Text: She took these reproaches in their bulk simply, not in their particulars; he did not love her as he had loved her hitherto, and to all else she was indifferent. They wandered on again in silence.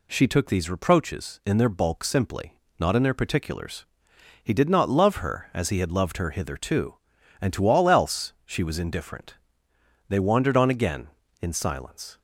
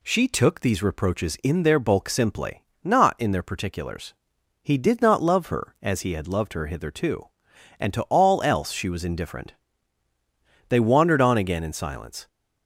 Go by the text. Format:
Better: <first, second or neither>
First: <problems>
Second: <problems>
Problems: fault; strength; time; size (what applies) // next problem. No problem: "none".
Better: neither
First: none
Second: none